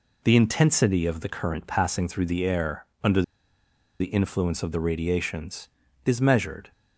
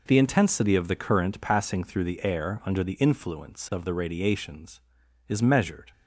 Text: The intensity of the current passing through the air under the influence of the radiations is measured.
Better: second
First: pauses between "air" and "under"; slight; at 2.8 s; 0.18 s long // pauses between "under" and "the"; noticeable; at 3.2 s; 0.77 s long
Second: none

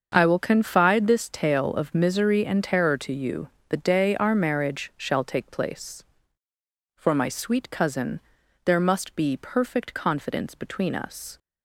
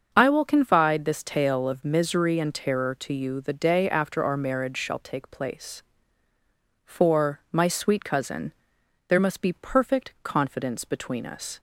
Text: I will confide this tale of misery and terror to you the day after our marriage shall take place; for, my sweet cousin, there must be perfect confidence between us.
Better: second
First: starts louder than the rest; until 1.1 s; 7 dB // pauses between "you" and "the"; slight; at 3.4 s; 0.22 s long // skips "after"; at 4.1 s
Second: starts louder than the rest; until 1.1 s; 6.5 dB

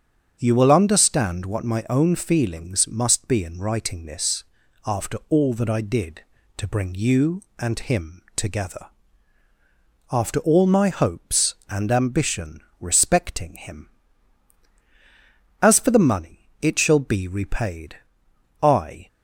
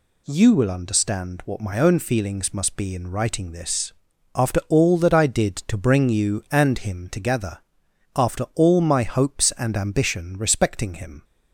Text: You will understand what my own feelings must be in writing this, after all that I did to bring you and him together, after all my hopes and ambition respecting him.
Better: second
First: starts louder than the rest; strong; until 1.4 s; 7 dB // pauses between "ambition" and "respecting"; slight; at 12.5 s; 0.20 s long // goes on to say "As for the money it shall be repaid I"; strong; from 15.5 s on; 3.4 s long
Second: none

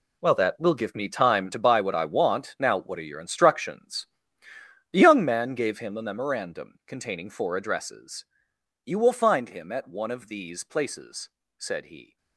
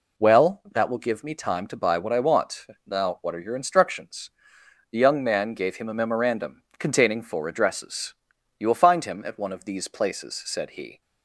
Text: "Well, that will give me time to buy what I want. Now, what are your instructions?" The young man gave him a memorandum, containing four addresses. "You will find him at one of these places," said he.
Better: second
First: gets quieter; strong; throughout; 12.5 dB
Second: none

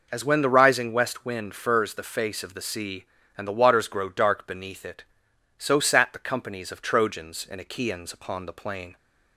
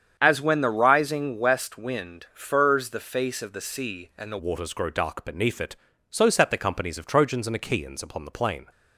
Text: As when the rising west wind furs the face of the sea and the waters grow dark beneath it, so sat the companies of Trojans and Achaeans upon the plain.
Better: first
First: none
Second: starts louder than the rest; strong; until 1.1 s; 8 dB // changes voice at "waters"; from 4.3 s on; 4.3 s long

